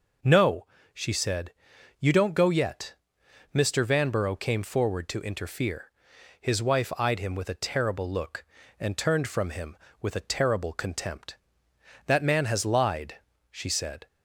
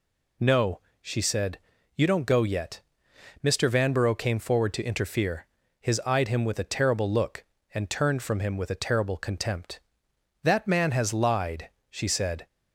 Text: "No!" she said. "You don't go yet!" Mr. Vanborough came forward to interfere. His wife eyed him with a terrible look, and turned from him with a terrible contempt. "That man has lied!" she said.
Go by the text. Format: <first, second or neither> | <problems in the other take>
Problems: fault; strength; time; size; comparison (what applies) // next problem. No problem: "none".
first | skips "wife"; at 6.0 s